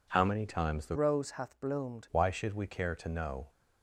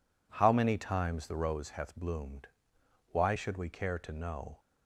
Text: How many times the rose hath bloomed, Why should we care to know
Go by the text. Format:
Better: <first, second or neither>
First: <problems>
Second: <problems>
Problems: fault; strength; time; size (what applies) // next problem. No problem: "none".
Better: second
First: changes voice from "rose" to "bloomed"; from 0.9 to 2.0 s; 1.1 s long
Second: none